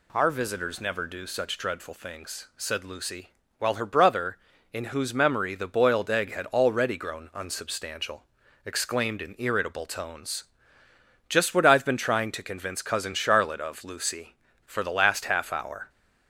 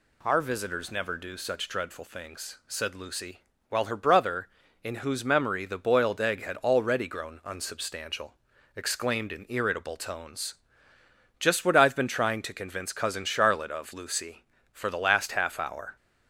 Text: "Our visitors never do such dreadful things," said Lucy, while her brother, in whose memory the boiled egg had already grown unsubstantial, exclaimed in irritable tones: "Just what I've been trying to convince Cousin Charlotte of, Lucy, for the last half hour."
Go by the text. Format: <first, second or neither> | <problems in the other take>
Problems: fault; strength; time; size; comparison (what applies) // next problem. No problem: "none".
neither | none